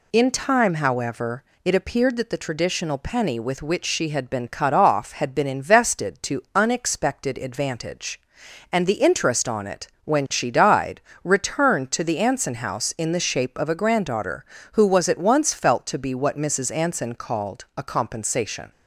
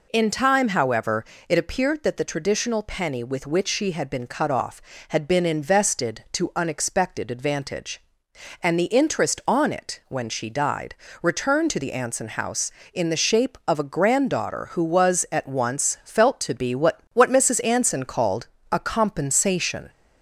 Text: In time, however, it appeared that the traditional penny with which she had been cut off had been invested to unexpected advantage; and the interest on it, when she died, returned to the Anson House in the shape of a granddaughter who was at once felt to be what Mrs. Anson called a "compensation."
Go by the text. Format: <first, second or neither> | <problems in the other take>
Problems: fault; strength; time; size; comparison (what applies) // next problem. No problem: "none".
first | says "what" twice; at 17.1 s // pauses between "called" and "a"; slight; at 18.4 s; 0.24 s long